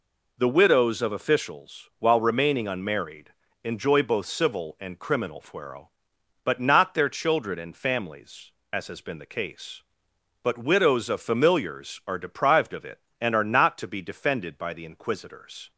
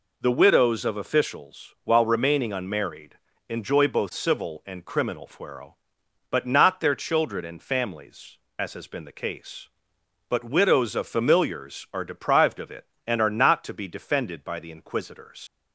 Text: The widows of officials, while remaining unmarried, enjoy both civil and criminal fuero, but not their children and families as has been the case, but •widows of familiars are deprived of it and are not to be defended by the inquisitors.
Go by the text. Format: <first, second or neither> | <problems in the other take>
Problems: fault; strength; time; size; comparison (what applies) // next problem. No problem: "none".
first | leaves "inquisitors" unfinished; at 15.4 s; 100 ms